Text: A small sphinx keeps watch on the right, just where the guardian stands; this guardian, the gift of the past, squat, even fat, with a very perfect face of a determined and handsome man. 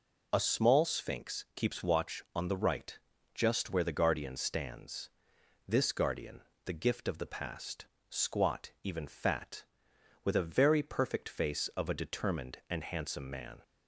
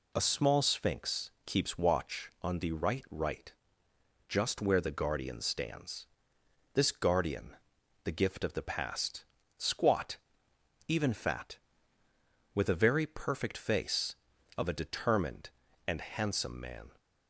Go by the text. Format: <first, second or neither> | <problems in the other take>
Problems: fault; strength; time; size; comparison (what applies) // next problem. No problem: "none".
first | says "right" twice; at 3.1 s